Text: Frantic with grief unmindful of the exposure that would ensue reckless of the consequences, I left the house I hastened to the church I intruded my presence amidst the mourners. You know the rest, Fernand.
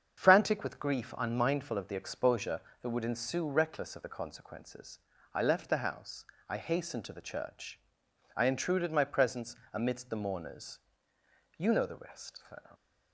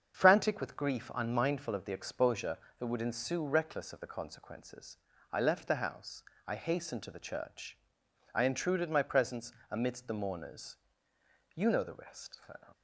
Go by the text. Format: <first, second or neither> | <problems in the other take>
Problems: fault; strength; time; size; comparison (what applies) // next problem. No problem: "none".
neither | starts louder than the rest; strong; the same in both // pauses between "house" and "I"; slight; the same in both // pauses between "church" and "I"; noticeable; the same in both // pauses between "presence" and "amidst"; slight; the same in both